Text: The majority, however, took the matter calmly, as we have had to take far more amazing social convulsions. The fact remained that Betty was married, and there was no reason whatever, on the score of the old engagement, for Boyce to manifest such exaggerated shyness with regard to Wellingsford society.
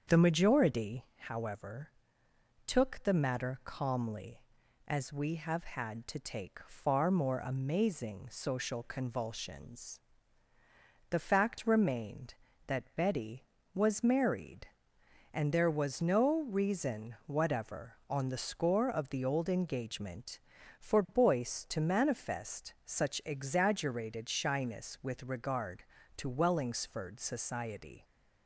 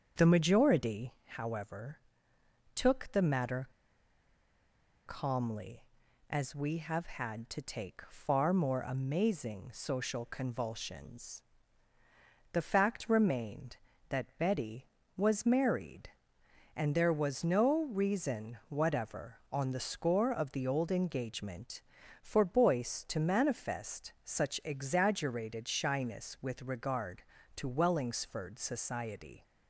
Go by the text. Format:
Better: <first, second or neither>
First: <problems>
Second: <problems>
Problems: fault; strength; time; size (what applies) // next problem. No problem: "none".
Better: first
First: starts louder than the rest; strong; until 1.2 s; 7 dB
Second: starts louder than the rest; strong; until 1.2 s; 7 dB // pauses between "matter" and "calmly"; strong; at 3.6 s; 1.3 s long